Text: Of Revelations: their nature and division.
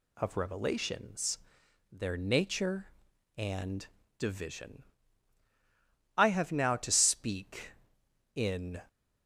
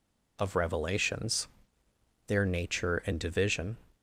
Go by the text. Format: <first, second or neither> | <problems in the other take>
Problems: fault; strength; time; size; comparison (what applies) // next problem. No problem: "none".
second | pauses between "and" and "division"; slight; at 3.8 s; 0.32 s long // goes on to say "I HAVE now to speak in"; strong; from 6.1 s on; 2.6 s long